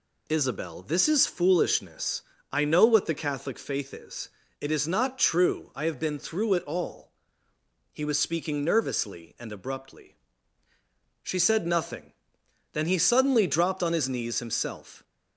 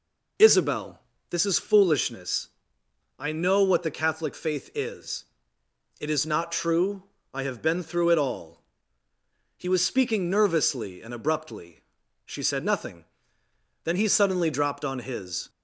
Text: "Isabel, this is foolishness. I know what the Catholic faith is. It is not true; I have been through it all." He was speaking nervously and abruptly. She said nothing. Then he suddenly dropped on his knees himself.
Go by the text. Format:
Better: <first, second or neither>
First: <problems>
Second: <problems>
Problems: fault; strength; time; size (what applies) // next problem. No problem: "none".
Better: first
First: none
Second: stops before "knees himself"; at 15.4 s